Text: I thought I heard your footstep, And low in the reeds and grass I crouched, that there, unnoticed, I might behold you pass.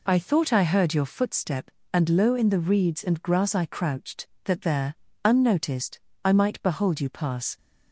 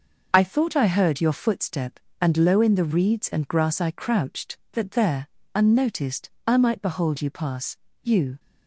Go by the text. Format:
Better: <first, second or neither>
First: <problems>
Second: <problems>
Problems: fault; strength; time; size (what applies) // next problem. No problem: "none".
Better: first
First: none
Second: goes on to say "You"; slight; from 8.0 s on; 0.38 s long